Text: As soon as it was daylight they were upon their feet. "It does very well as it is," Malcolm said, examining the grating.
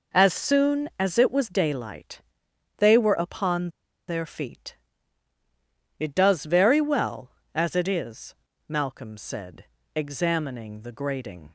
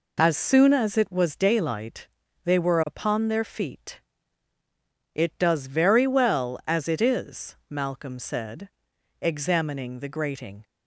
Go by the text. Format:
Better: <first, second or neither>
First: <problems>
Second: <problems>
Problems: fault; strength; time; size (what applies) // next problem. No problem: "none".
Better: second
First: pauses between "daylight" and "they"; noticeable; at 2.1 s; 0.58 s long // pauses between "upon" and "their"; at 3.6 s; 0.38 s long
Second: pauses between "daylight" and "they"; slight; at 2.0 s; 0.34 s long